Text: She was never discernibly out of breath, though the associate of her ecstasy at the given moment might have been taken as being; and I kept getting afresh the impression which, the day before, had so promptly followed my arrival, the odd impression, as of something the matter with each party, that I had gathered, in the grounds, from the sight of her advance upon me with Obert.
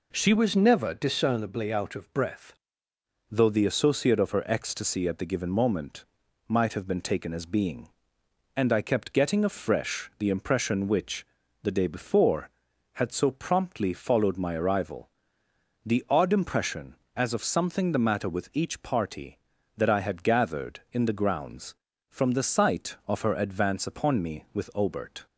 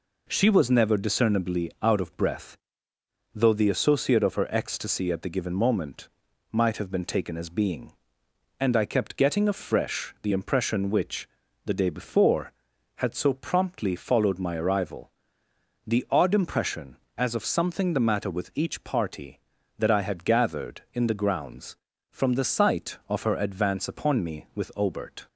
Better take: second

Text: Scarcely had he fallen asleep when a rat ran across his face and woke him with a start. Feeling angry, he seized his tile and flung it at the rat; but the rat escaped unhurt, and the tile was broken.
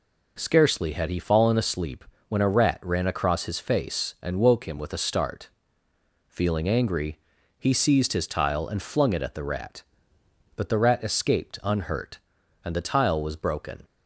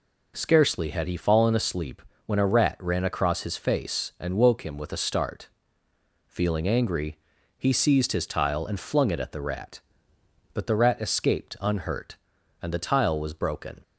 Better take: neither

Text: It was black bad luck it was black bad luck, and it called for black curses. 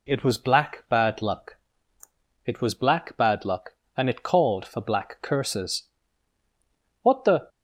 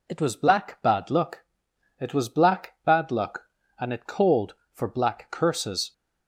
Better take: second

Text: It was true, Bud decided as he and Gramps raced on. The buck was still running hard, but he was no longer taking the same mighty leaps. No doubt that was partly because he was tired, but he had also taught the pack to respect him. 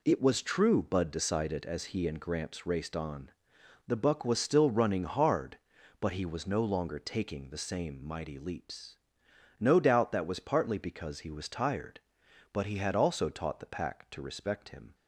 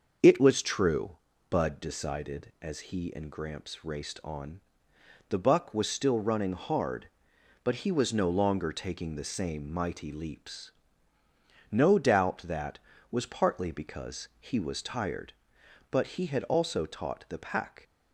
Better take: first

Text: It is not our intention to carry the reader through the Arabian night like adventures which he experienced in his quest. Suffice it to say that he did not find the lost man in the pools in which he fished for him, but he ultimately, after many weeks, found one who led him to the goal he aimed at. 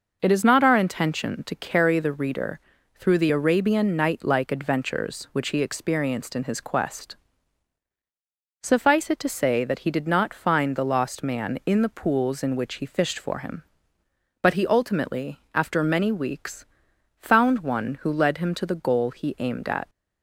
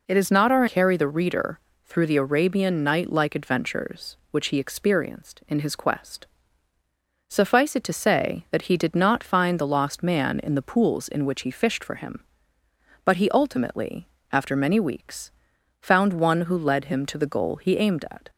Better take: first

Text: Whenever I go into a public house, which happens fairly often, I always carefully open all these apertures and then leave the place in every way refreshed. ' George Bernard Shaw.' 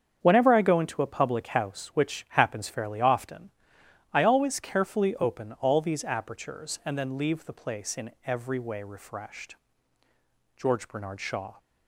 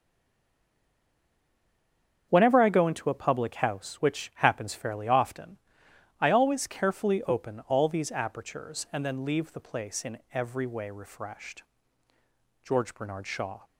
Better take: first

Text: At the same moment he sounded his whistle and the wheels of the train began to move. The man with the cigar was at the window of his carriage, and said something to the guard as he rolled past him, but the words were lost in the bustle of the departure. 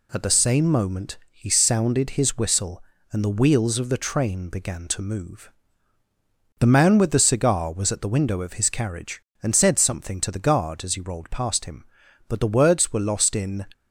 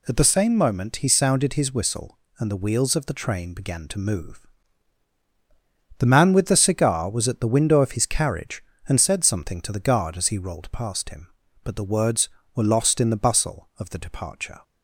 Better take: second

